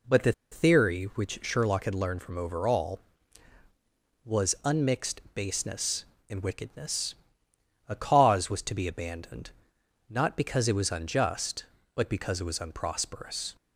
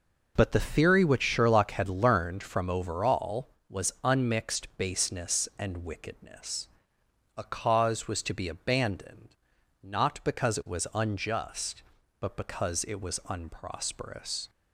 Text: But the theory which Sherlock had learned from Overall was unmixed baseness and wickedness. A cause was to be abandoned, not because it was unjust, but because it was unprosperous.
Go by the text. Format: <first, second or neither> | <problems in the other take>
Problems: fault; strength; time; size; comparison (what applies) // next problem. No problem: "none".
second | pauses between "the" and "theory"; slight; at 0.3 s; 0.19 s long